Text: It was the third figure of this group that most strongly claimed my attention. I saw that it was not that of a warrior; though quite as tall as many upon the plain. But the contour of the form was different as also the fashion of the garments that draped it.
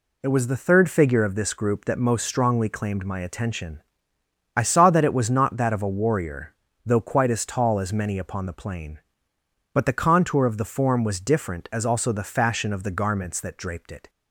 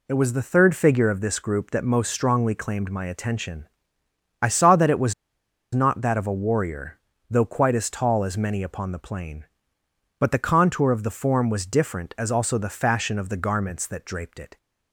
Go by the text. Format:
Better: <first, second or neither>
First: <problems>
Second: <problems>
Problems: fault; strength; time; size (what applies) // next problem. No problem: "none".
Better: first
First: none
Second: pauses between "was" and "not"; noticeable; at 5.1 s; 0.59 s long